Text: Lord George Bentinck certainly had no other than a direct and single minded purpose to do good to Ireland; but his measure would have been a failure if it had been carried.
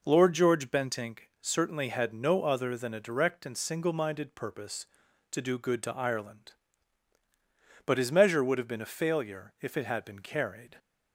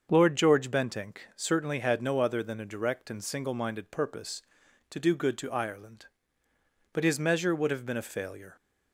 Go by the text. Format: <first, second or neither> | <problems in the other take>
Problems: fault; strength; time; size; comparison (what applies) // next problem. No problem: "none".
first | starts louder than the rest; until 1.1 s; 6.5 dB // stops before "if it had been carried"; at 8.5 s